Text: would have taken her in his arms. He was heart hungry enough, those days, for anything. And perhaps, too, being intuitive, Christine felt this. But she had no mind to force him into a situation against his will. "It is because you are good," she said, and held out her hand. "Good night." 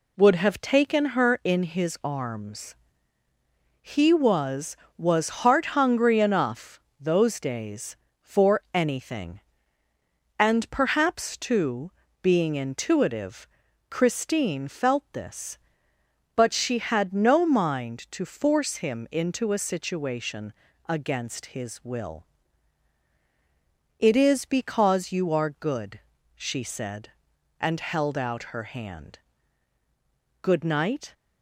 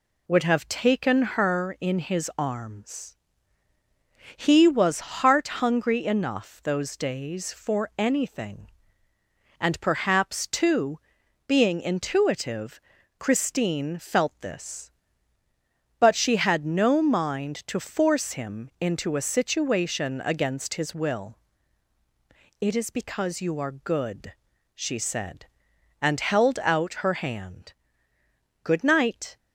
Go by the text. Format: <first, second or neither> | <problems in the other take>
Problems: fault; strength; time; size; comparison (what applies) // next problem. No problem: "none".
second | says "was" twice; at 4.9 s // pauses between "situation" and "against"; slight; at 20.5 s; 0.36 s long